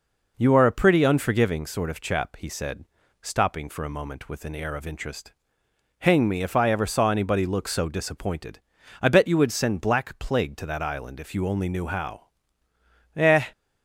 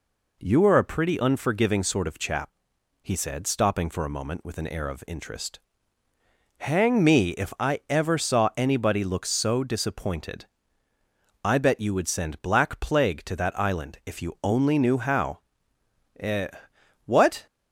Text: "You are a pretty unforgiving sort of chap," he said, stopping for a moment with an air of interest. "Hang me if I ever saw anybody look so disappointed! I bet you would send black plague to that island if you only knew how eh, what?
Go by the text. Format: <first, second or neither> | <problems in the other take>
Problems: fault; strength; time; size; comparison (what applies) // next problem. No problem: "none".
second | pauses between "how" and "eh"; noticeable; at 12.2 s; 0.88 s long; noticeable in the second // stops before "what"; at 13.5 s